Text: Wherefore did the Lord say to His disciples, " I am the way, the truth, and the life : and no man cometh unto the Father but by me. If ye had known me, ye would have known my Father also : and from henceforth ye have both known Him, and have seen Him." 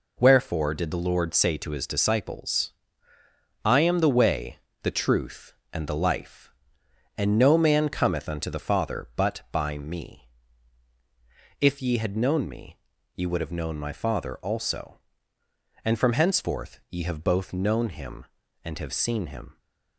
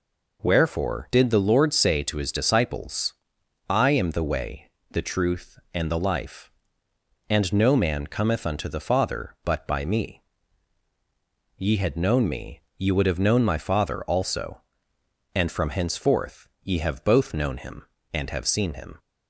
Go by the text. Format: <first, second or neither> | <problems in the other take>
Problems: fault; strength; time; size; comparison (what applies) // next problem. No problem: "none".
first | skips "If"; at 10.9 s